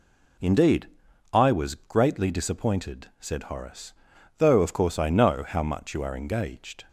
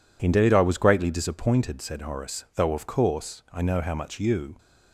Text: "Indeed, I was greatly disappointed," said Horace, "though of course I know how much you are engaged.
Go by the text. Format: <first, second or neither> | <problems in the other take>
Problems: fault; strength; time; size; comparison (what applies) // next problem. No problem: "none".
first | stops before "are engaged"; at 4.5 s